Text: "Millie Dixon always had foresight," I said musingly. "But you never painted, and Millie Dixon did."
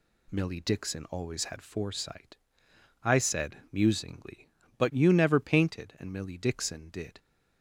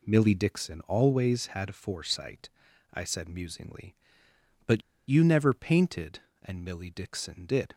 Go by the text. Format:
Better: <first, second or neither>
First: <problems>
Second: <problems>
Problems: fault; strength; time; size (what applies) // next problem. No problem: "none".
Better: first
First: none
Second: pauses between "But" and "you"; slight; at 4.8 s; 0.26 s long